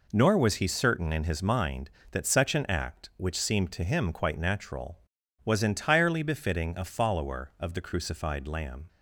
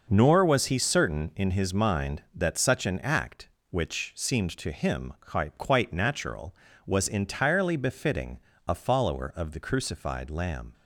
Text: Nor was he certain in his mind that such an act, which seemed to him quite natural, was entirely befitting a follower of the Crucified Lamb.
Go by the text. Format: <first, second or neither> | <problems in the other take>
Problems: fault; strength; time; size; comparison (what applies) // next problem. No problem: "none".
first | says "quite" twice; at 5.5 s // pauses between "befitting" and "a"; slight; at 8.3 s; 0.28 s long